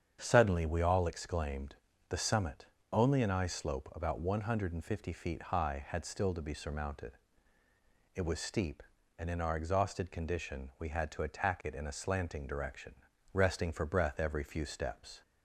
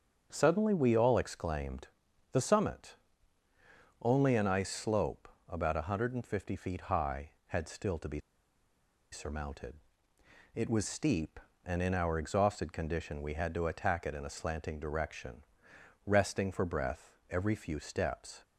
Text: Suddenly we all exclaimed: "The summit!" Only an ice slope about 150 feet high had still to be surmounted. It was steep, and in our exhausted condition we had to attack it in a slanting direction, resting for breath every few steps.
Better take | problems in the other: first | starts louder than the rest; until 1.3 s; 7 dB; strong in the first // pauses between "slope" and "about"; slight; at 5.2 s; 0.22 s long // pauses between "be" and "surmounted"; noticeable; at 8.2 s; 0.92 s long

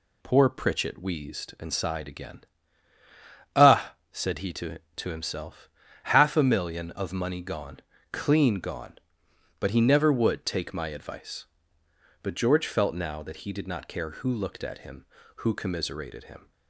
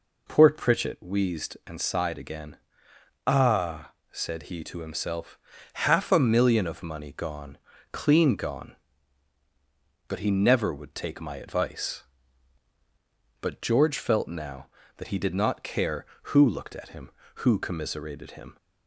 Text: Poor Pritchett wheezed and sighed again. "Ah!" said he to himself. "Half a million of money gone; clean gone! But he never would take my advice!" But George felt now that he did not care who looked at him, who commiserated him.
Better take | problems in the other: second | says "to" twice; at 4.9 s

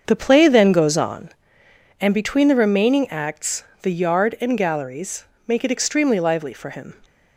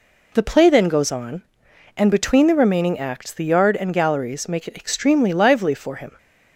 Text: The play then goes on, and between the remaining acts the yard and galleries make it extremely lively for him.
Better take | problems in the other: second | starts louder than the rest; until 1.5 s; 6.5 dB // pauses between "acts" and "the"; slight; at 3.6 s; 0.20 s long // pauses between "galleries" and "make"; slight; at 5.2 s; 0.24 s long

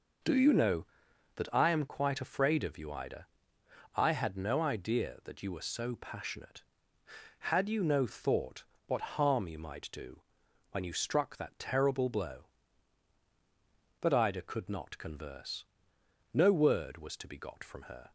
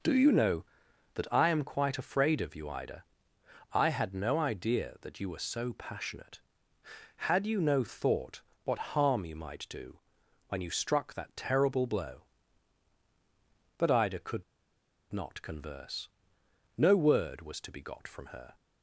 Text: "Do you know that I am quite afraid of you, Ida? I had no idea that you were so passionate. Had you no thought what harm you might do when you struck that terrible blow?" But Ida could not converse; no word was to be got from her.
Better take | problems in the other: first | pauses between "thought" and "what"; slight; at 8.4 s; 0.22 s long; slight in the first // pauses between "do" and "when"; noticeable; at 9.9 s; 0.50 s long; noticeable in the first // pauses between "could" and "not"; noticeable; at 14.4 s; 0.69 s long

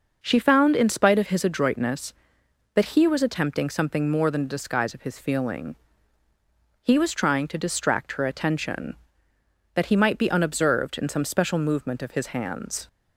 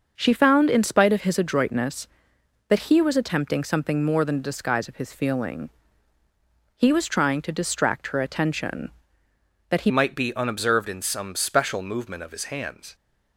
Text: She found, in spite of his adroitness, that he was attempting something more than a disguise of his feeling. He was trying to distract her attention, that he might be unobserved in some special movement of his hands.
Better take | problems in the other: first | starts louder than the rest; until 1.1 s; 6.5 dB // changes voice at "might"; from 9.8 s on; 3.1 s long

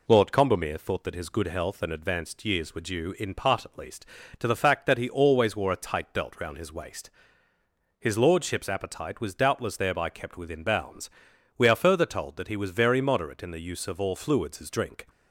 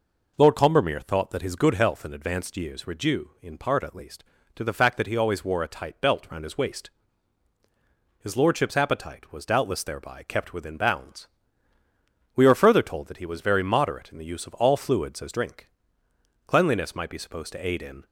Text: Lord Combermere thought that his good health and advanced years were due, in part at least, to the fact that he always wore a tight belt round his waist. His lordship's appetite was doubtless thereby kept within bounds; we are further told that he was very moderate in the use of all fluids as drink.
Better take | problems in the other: first | goes on to say "Cleanliness might be supposed to aid in"; from 16.4 s on; 1.5 s long

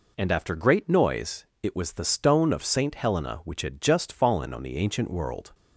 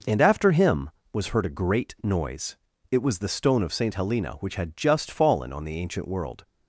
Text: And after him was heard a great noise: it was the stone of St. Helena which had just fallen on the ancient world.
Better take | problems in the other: second | skips "him was heard a"; at 0.5 s

